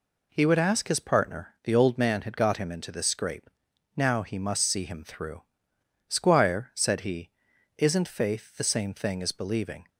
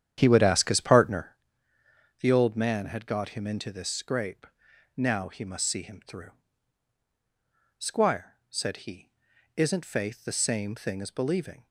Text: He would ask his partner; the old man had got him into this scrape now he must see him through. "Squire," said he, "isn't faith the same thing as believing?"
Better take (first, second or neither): first